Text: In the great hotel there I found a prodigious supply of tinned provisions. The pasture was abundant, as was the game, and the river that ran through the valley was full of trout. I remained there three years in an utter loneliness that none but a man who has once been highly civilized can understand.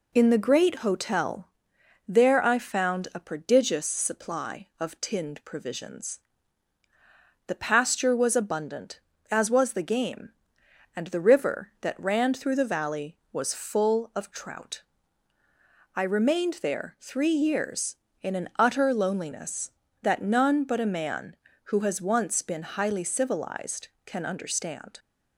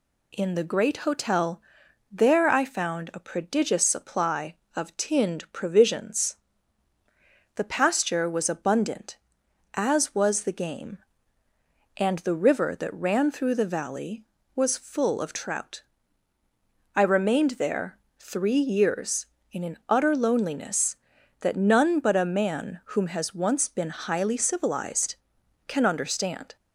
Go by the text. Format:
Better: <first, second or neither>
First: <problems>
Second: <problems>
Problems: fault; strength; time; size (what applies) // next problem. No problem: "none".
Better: first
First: pauses between "hotel" and "there"; noticeable; at 1.4 s; 0.58 s long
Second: pauses between "hotel" and "there"; noticeable; at 1.6 s; 0.50 s long // pauses between "there" and "three"; slight; at 17.9 s; 0.20 s long // says "whom" for "who"; at 22.8 s